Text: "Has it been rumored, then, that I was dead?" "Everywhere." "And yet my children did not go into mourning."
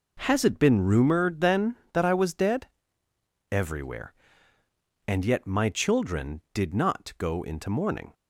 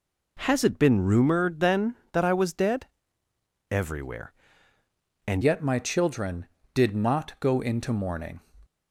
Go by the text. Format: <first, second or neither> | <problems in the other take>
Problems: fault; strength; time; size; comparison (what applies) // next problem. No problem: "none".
first | changes voice at "yet"; from 5.4 s on; 3.0 s long